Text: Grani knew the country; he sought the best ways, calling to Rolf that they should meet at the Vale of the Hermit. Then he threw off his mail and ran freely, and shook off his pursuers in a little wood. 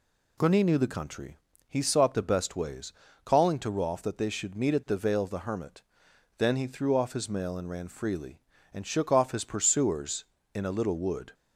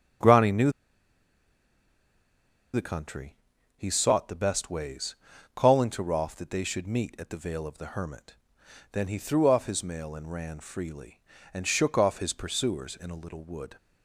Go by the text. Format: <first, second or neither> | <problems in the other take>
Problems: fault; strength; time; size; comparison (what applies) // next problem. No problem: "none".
first | starts louder than the rest; strong; until 3.2 s; 7.5 dB // pauses between "knew" and "the"; strong; at 0.6 s; 2.0 s long